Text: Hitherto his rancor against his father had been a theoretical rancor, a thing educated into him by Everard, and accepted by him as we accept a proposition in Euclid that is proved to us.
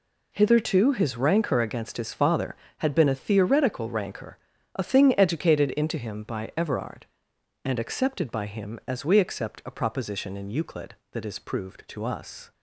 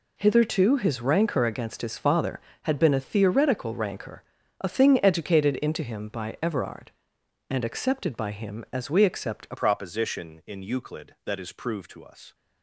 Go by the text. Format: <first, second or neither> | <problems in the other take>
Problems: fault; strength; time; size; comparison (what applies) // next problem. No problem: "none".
first | changes voice at "proposition"; from 9.5 s on; 2.8 s long